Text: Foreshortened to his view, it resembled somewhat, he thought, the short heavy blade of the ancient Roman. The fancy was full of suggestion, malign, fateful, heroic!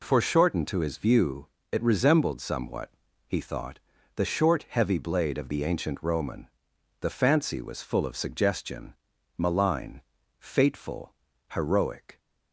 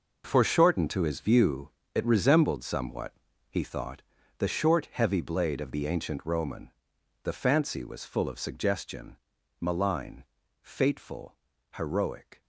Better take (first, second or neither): first